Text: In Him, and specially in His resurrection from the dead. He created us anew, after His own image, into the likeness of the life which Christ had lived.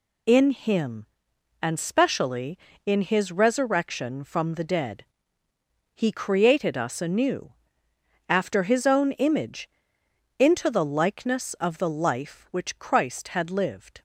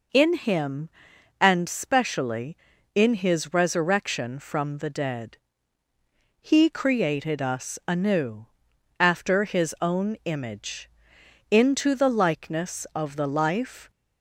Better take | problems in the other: first | stops before "which Christ had lived"; at 13.8 s

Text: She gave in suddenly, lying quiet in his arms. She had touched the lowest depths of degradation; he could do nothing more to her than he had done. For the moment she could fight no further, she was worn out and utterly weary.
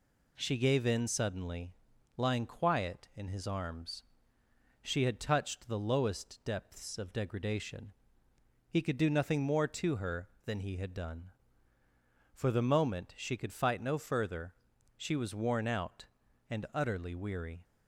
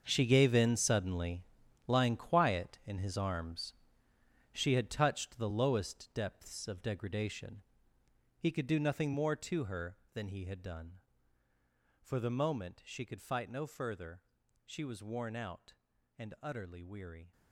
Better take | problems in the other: first | gets quieter; strong; throughout; 13.5 dB

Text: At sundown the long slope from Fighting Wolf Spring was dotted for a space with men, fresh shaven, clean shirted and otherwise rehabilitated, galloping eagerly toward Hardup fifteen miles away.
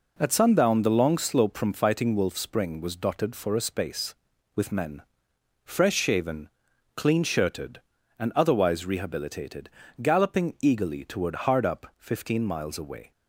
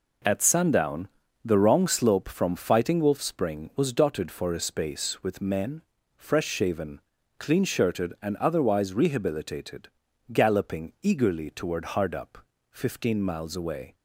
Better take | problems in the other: first | pauses between "sundown" and "the"; slight; at 1.0 s; 0.36 s long // says "wrong" for "long"; at 1.5 s // pauses between "Hardup" and "fifteen"; slight; at 12.3 s; 0.34 s long

